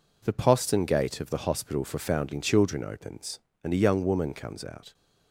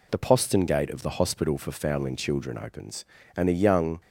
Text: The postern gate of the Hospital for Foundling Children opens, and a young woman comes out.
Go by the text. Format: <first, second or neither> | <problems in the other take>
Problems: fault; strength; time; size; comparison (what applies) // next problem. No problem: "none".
first | stops before "woman comes out"; at 4.0 s